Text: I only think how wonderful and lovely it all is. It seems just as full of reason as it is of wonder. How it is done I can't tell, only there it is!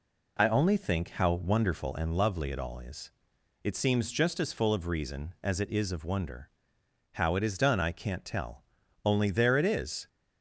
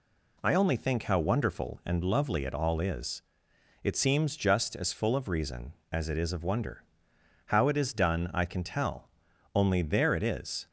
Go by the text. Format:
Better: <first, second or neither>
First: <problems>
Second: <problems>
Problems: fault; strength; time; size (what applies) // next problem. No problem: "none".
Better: first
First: none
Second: says "can" for "can't"; at 8.4 s